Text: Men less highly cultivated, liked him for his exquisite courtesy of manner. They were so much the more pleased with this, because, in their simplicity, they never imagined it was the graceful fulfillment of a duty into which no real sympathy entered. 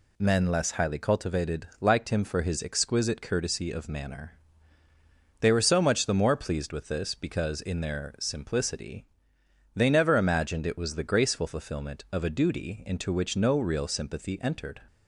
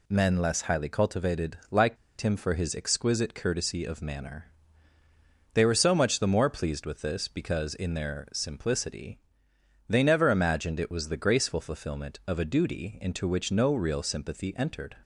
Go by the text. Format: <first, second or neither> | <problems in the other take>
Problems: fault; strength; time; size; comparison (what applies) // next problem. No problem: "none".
first | pauses between "liked" and "him"; slight; at 1.9 s; 0.25 s long